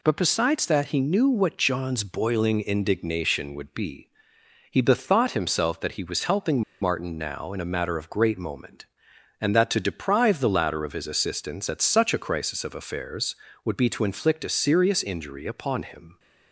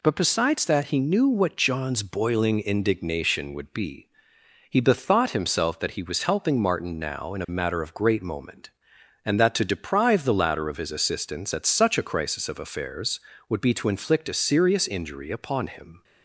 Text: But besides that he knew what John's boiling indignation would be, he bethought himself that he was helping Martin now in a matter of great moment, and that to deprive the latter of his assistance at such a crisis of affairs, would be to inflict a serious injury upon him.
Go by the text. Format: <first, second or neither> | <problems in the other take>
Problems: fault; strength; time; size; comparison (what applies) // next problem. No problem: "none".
second | pauses between "helping" and "Martin"; slight; at 6.6 s; 0.20 s long